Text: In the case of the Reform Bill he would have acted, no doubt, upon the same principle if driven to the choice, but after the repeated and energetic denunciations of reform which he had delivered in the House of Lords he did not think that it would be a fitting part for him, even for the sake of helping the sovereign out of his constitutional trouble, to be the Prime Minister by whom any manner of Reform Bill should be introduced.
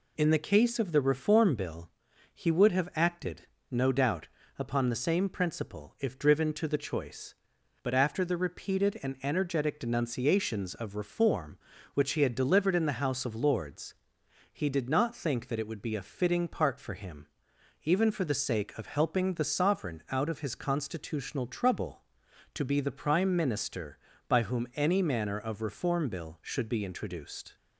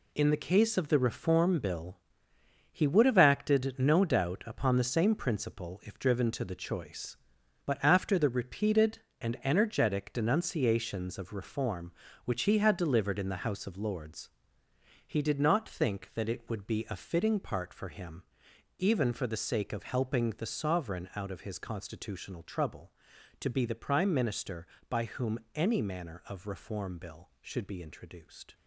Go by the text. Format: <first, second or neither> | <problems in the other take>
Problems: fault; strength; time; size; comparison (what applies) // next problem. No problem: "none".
first | gets quieter; strong; throughout; 8.5 dB // pauses between "Bill" and "he"; noticeable; at 1.9 s; 0.76 s long; also in the first // pauses between "Lords" and "he"; noticeable; at 14.3 s; 0.76 s long; noticeable in the first // pauses between "whom" and "any"; slight; at 25.3 s; 0.16 s long